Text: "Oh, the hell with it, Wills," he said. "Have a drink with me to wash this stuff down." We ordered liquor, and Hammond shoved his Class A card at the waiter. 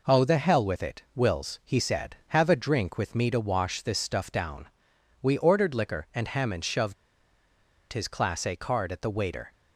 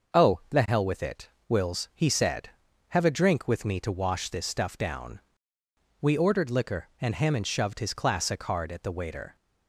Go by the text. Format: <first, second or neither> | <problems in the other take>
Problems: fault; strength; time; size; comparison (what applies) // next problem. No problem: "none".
second | pauses between "shoved" and "his"; noticeable; at 6.9 s; 0.95 s long